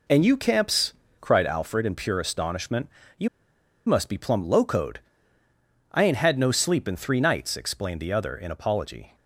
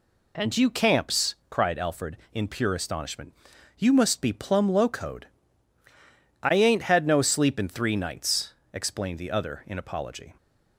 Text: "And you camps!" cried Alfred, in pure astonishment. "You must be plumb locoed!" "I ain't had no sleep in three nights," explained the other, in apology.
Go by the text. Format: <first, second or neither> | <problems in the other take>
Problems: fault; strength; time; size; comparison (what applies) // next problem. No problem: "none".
second | pauses between "You" and "must"; noticeable; at 3.2 s; 0.58 s long